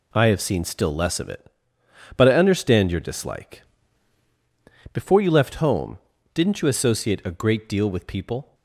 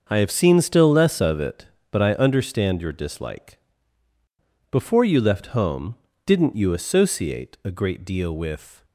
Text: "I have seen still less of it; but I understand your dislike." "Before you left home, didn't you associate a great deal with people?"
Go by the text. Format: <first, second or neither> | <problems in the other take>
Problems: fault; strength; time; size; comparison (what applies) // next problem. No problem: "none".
first | starts louder than the rest; until 1.0 s; 6.5 dB // stops before "people"; at 8.8 s